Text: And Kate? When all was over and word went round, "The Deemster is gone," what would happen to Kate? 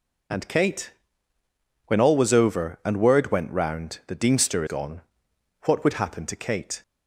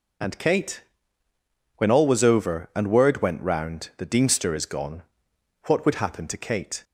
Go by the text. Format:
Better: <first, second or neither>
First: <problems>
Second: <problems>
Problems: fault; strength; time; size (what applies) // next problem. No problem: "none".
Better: second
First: skips "is"; at 4.6 s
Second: none